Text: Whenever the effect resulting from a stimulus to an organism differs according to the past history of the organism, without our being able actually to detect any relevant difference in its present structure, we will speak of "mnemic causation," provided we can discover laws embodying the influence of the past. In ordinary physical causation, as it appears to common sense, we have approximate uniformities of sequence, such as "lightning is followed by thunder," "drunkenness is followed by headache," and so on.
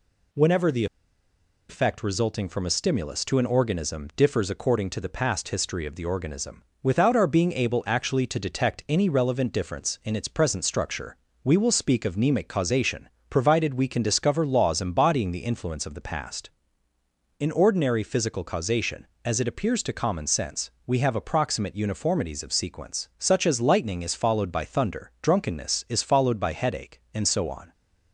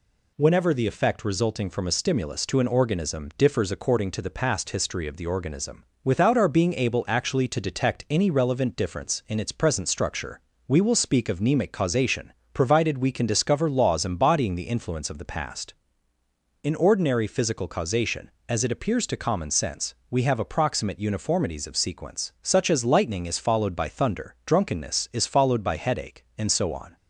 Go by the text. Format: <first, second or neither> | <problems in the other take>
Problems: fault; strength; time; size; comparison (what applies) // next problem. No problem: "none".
second | pauses between "the" and "effect"; noticeable; at 0.8 s; 0.84 s long